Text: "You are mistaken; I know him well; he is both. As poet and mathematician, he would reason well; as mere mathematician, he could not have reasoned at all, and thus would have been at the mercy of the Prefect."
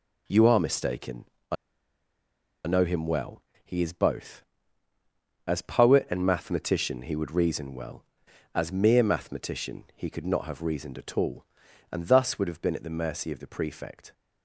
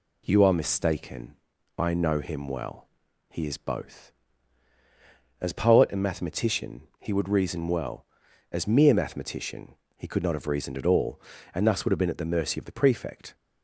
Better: second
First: pauses between "I" and "know"; at 1.5 s; 1.1 s long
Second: none

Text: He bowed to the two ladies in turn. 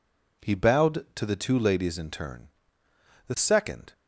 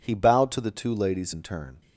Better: second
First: goes on to say "The second"; noticeable; from 3.2 s on; 0.65 s long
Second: none

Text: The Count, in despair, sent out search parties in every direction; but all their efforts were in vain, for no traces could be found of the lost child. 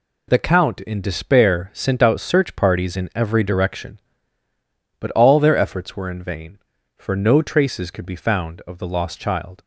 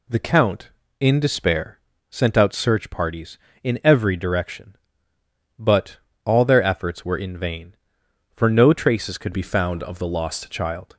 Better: first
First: none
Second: pauses between "but" and "all"; slight; at 5.9 s; 0.26 s long // changes voice from "be" to "lost"; from 9.3 to 10.5 s; 1.2 s long

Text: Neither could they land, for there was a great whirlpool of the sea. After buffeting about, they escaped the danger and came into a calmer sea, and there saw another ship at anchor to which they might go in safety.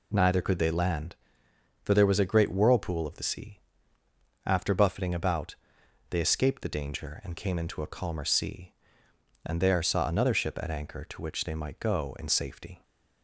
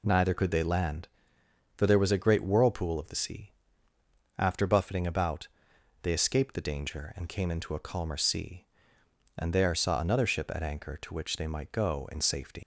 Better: first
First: none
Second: leaves "safety" unfinished; at 12.6 s; 115 ms

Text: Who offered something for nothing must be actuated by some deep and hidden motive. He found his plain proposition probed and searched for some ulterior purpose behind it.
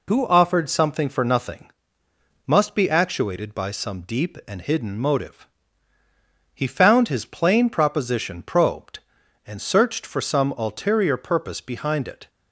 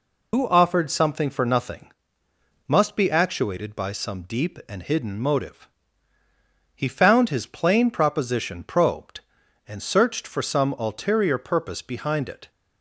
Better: first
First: pauses between "nothing" and "must"; noticeable; at 1.6 s; 0.78 s long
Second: loses the start of "Who"; at 0.3 s; 40 ms // pauses between "nothing" and "must"; noticeable; at 1.8 s; 0.78 s long

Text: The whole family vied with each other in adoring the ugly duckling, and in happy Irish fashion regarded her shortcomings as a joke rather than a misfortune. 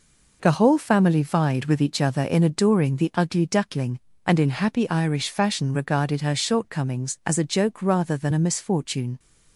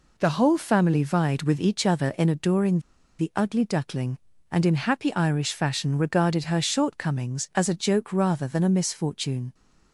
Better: first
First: none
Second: pauses between "adoring" and "the"; at 2.7 s; 0.40 s long

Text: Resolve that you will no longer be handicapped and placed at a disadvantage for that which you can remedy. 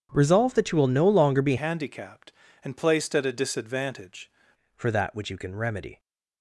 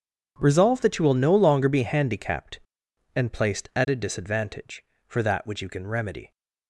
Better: second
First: starts louder than the rest; strong; until 1.1 s; 8 dB // changes voice from "handicapped" to "disadvantage"; from 1.5 to 4.2 s; 2.7 s long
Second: starts louder than the rest; strong; until 1.3 s; 8 dB

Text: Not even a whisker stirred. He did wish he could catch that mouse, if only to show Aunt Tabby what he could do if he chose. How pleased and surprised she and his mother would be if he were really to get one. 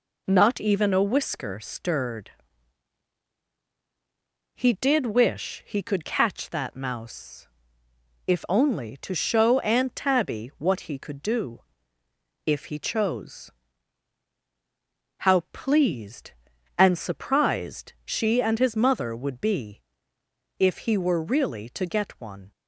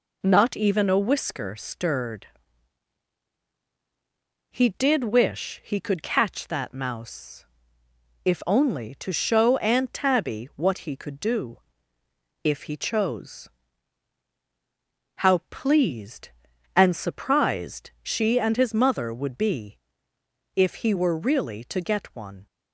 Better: neither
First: pauses between "do" and "if"; noticeable; at 11.6 s; 0.84 s long // pauses between "be" and "if"; noticeable; at 19.8 s; 0.78 s long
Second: pauses between "do" and "if"; noticeable; at 11.5 s; 0.84 s long // pauses between "be" and "if"; noticeable; at 19.7 s; 0.78 s long

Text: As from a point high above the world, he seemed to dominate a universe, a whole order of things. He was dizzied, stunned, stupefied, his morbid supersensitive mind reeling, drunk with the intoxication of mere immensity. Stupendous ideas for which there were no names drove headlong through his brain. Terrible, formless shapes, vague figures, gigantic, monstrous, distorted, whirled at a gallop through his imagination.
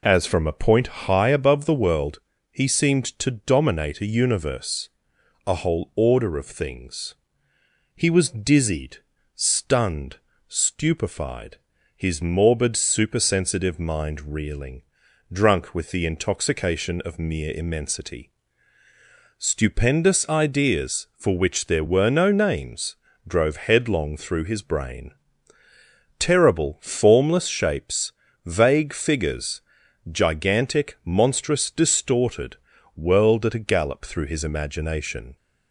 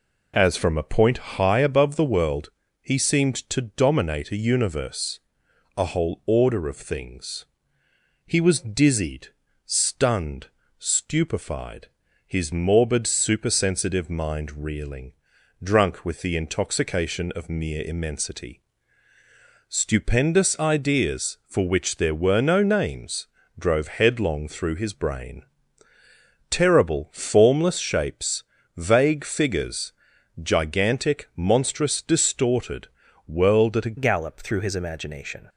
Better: first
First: pauses between "names" and "drove"; slight; at 22.9 s; 0.30 s long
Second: pauses between "names" and "drove"; slight; at 23.2 s; 0.30 s long // changes voice at "gallop"; from 33.9 s on; 1.5 s long

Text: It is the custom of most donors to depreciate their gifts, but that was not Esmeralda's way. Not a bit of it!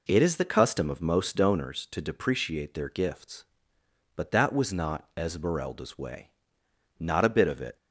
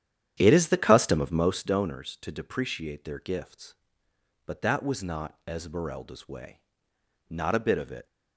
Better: first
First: none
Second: starts louder than the rest; strong; until 1.7 s; 10 dB

